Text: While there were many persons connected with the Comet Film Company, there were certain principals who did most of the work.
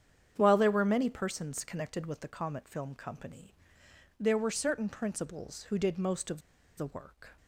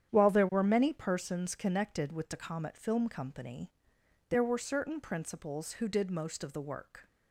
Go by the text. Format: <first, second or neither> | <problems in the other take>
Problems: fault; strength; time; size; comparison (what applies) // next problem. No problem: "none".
second | starts louder than the rest; strong; until 1.3 s; 8.5 dB; strong in the second // pauses between "of" and "the"; at 6.4 s; 0.37 s long